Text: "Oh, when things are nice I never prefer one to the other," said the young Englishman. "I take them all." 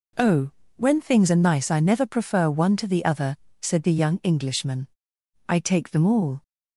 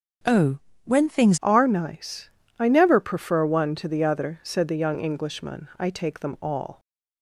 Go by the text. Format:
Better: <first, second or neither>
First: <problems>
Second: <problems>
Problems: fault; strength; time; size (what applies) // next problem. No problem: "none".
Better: first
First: none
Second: starts louder than the rest; until 1.5 s; 6 dB // changes voice at "are"; from 1.4 s on; 5.3 s long // pauses between "nice" and "I"; slight; at 2.2 s; 0.28 s long